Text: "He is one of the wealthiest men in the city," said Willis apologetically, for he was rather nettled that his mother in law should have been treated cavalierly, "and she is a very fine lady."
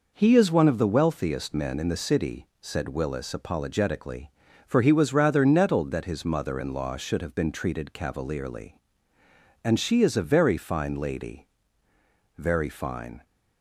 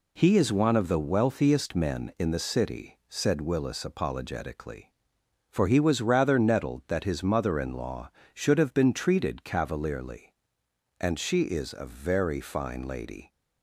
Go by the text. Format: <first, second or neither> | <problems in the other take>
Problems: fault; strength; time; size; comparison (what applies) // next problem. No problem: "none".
second | goes on to say "Very fine"; noticeable; from 12.3 s on; 0.88 s long